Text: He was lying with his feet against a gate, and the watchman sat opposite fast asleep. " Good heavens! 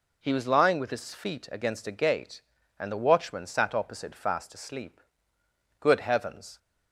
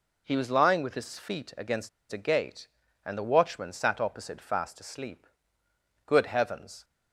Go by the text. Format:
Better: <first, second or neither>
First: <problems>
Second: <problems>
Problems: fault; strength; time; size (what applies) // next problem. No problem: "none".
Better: first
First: none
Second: pauses between "against" and "a"; slight; at 1.8 s; 0.22 s long